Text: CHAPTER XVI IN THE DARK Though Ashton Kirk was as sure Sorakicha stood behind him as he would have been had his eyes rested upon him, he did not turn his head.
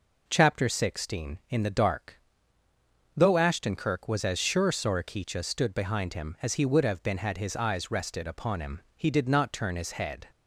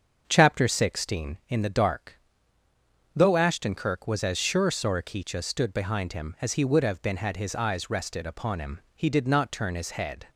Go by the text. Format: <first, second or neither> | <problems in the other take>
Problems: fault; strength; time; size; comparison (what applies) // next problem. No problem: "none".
first | starts louder than the rest; until 1.4 s; 6.5 dB // pauses between "DARK" and "Though"; noticeable; at 2.1 s; 0.96 s long; noticeable in the first